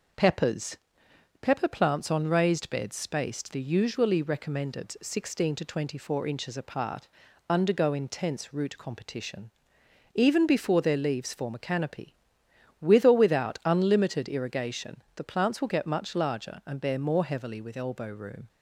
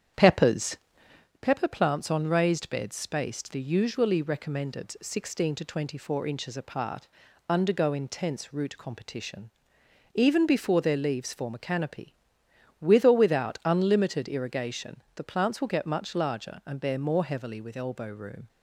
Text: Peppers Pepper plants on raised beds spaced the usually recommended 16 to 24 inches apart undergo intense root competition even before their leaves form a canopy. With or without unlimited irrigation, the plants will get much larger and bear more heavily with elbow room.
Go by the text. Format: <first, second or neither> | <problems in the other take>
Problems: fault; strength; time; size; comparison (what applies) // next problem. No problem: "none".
first | starts louder than the rest; strong; until 1.3 s; 9 dB // pauses between "Peppers" and "Pepper"; noticeable; at 0.7 s; 0.66 s long; noticeable in the first // pauses between "apart" and "undergo"; at 7.0 s; 0.42 s long; also in the first // pauses between "competition" and "even"; noticeable; at 9.4 s; 0.64 s long; noticeable in the first